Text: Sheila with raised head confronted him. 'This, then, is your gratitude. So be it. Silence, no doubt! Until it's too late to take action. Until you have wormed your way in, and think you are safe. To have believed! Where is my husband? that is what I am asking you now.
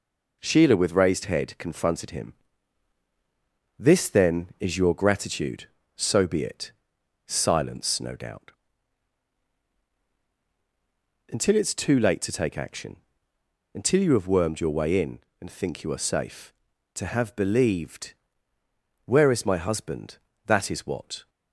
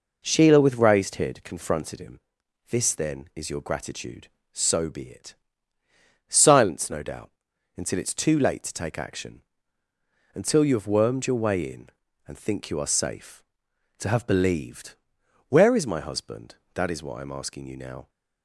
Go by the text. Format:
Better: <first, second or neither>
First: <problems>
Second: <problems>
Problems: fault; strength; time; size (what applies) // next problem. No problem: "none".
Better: second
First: stops before "I am asking you now"; at 21.2 s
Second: none